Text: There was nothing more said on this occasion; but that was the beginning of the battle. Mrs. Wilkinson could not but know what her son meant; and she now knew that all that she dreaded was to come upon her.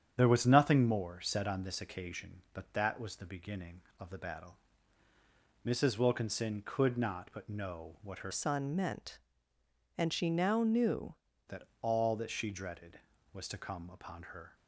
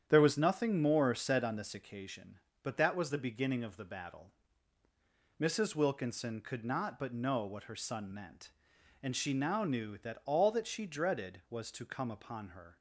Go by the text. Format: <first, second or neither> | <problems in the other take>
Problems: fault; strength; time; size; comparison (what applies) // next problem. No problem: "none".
second | starts louder than the rest; strong; until 1.1 s; 8.5 dB; strong in the second // changes voice from "son" to "knew"; from 8.3 to 11.1 s; 2.8 s long // pauses between "that" and "all"; slight; at 11.6 s; 0.18 s long